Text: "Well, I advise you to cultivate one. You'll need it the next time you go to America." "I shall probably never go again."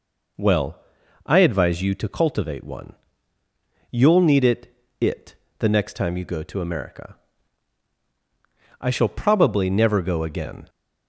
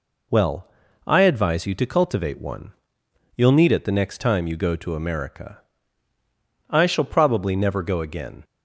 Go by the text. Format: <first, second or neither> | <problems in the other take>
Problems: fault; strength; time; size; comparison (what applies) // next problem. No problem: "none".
second | says "it" twice; at 4.9 s